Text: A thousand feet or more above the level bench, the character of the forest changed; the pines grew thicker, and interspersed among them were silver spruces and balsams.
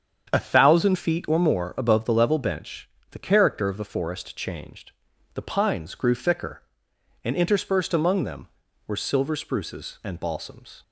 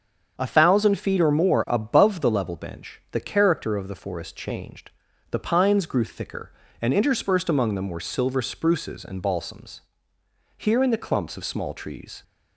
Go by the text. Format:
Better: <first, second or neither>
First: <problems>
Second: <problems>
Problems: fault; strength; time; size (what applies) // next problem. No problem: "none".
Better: first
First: starts louder than the rest; strong; until 1.3 s; 7.5 dB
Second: starts louder than the rest; strong; until 1.4 s; 7 dB // goes on to say "Here in the clumps of small trees"; strong; from 10.5 s on; 1.6 s long